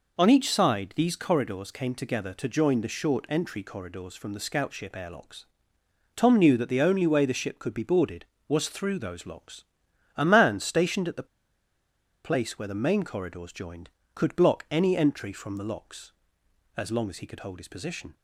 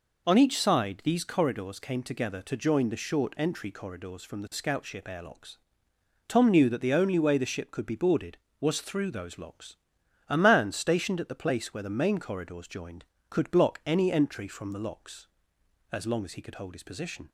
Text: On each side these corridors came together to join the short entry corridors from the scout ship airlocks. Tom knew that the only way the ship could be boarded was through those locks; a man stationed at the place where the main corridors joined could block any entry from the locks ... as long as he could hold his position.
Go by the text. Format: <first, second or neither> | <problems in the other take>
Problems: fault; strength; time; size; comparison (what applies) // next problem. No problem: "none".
second | pauses between "the" and "place"; at 11.2 s; 0.99 s long